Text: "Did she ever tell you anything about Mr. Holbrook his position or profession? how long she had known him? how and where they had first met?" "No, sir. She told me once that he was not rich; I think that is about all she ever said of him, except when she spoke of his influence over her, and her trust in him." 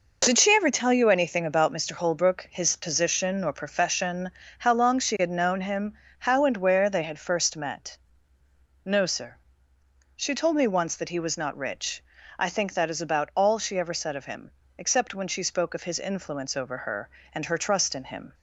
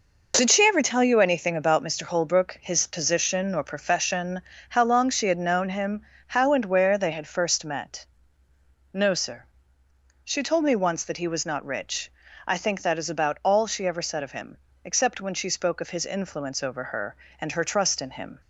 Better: neither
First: none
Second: none

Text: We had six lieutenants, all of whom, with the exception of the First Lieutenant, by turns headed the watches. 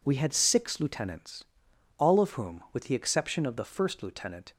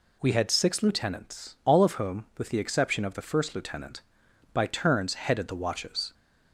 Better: second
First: stops before "by turns headed the watches"; at 4.5 s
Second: none

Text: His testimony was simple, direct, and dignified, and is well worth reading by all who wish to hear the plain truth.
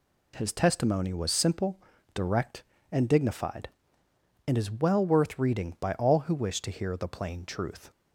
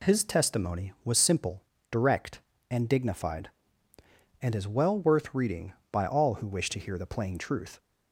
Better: neither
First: none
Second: none

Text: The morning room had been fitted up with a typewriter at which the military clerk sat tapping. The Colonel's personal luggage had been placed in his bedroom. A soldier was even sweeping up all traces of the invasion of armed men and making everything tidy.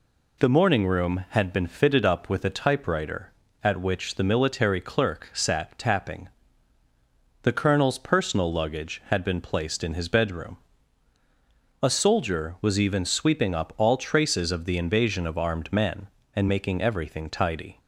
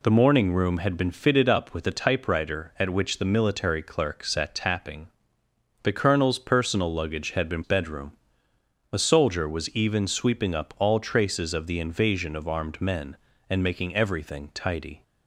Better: first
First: none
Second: skips "placed in his"; at 7.6 s

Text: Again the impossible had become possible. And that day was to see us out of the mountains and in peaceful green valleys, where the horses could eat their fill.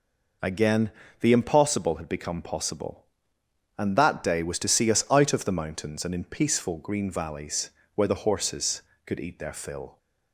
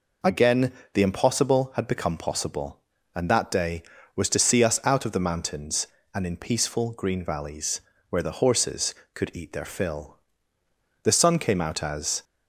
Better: first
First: pauses between "Again" and "the"; slight; at 0.9 s; 0.28 s long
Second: pauses between "Again" and "the"; slight; at 0.7 s; 0.22 s long // goes on to say "The sun came out as"; noticeable; from 11.0 s on; 1.2 s long

